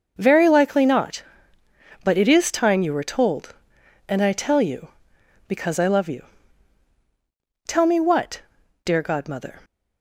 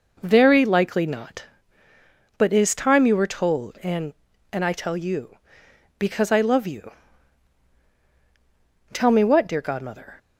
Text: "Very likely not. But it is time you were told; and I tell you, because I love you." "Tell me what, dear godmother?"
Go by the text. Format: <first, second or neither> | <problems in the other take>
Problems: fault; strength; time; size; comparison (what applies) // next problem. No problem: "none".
first | says "and" twice; at 4.5 s